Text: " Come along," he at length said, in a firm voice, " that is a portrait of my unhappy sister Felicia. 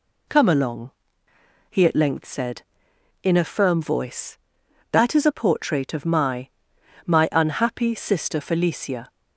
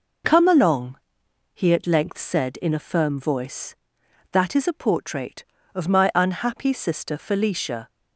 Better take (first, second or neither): second